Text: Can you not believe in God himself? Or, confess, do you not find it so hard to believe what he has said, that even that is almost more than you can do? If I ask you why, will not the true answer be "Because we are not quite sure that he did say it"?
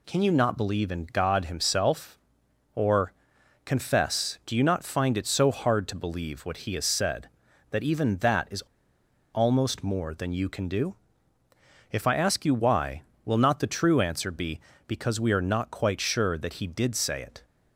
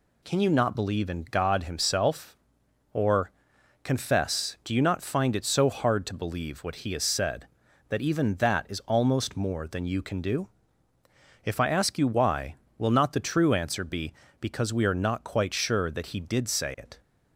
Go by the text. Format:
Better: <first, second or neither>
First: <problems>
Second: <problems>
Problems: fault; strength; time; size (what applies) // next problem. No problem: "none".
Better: second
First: pauses between "is" and "almost"; noticeable; at 8.6 s; 0.73 s long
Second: none